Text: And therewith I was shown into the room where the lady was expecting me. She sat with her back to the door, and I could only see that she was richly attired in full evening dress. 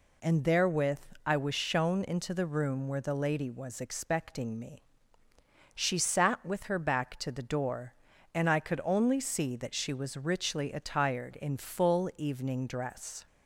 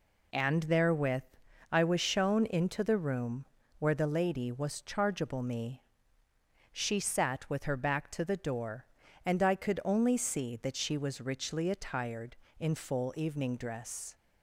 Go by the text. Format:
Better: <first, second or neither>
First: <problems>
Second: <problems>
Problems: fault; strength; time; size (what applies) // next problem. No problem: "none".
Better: first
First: pauses between "therewith" and "I"; slight; at 0.9 s; 0.24 s long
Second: pauses between "therewith" and "I"; noticeable; at 1.2 s; 0.48 s long // pauses between "room" and "where"; slight; at 3.4 s; 0.34 s long // says "chargeable" for "expecting"; at 4.8 s